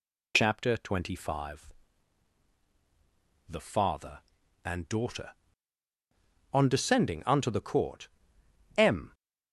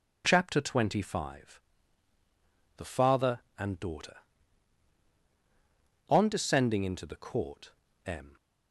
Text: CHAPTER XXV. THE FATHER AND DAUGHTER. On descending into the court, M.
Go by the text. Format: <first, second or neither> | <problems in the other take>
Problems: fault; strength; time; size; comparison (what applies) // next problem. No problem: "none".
second | says "unto" for "into"; at 7.2 s